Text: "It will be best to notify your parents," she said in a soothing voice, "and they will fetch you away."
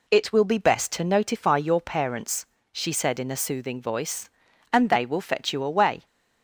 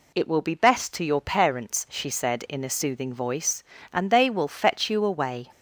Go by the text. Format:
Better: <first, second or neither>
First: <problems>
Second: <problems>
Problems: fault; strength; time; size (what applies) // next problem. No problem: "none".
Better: first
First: none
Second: skips "notify"; at 1.0 s